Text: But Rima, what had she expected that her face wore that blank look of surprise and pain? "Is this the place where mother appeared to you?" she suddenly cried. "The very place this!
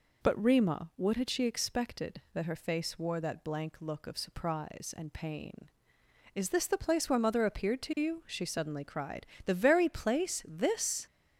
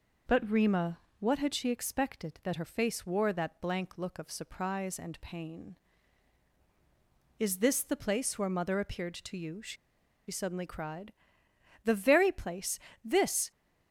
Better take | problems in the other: first | pauses between "she" and "suddenly"; noticeable; at 9.7 s; 0.54 s long // pauses between "place" and "this"; slight; at 12.7 s; 0.24 s long

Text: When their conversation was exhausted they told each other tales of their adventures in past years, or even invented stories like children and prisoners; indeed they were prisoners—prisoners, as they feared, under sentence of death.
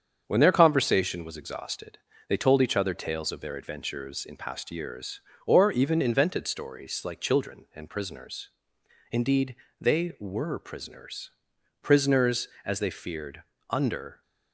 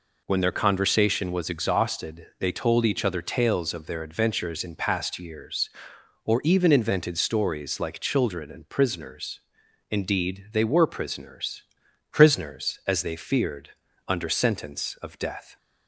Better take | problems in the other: second | starts louder than the rest; strong; until 1.2 s; 7.5 dB // pauses between "exhausted" and "they"; slight; at 1.9 s; 0.30 s long // pauses between "indeed" and "they"; slight; at 9.5 s; 0.24 s long // stops before "sentence of death"; at 14.2 s

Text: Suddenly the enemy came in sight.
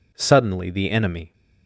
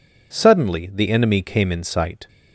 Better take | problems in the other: second | stops before "came in sight"; at 1.3 s

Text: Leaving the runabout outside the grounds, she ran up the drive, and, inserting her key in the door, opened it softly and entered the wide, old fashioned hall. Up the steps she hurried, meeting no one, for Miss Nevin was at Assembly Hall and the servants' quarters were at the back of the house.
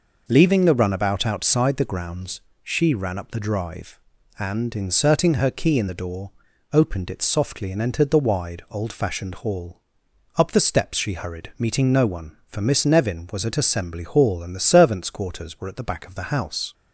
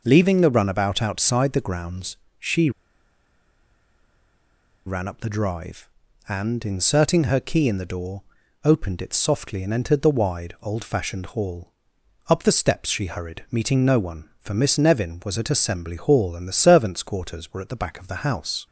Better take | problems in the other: first | pauses between "she" and "ran"; strong; at 2.7 s; 2.1 s long

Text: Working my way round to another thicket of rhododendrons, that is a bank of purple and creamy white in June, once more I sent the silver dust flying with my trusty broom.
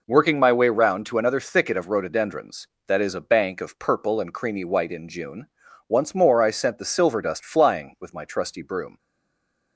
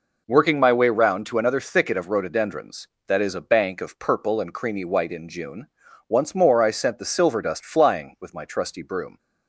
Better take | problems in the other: second | stays silent after the last word; slight; from 8.9 s on; 0.8 s long

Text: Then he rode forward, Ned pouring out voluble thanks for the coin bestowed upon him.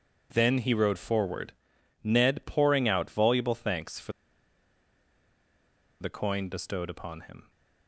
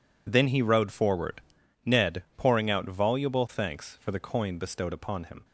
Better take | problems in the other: second | pauses between "for" and "the"; strong; at 4.1 s; 1.9 s long

